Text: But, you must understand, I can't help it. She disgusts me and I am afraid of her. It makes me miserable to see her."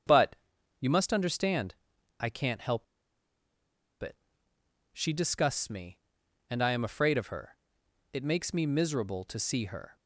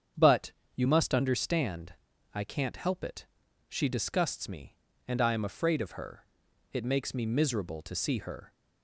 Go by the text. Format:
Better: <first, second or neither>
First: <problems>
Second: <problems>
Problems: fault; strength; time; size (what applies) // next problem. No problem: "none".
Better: second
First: starts louder than the rest; strong; until 1.5 s; 7.5 dB // pauses between "help" and "it"; at 2.8 s; 1.1 s long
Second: starts louder than the rest; strong; until 1.4 s; 8 dB